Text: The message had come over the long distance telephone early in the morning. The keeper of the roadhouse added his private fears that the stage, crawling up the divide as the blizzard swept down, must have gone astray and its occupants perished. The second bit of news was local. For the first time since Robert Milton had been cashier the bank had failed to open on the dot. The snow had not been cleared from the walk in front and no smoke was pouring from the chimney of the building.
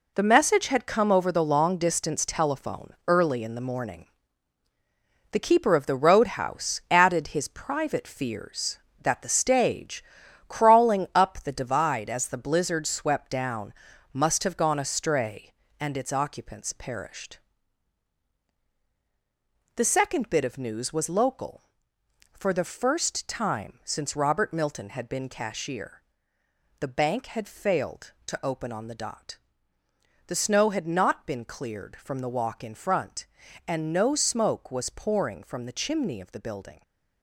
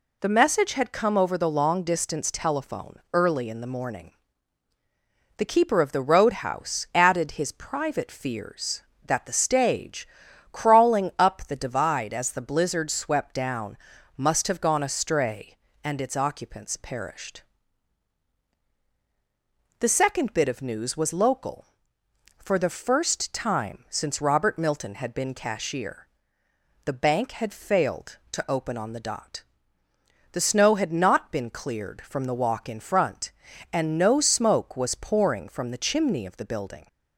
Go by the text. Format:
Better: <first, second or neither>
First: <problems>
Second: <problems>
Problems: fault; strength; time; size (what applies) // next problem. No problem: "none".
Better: second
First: gets quieter; strong; throughout; 8.5 dB // pauses between "cashier" and "the"; noticeable; at 26.0 s; 0.78 s long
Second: pauses between "cashier" and "the"; noticeable; at 26.0 s; 0.78 s long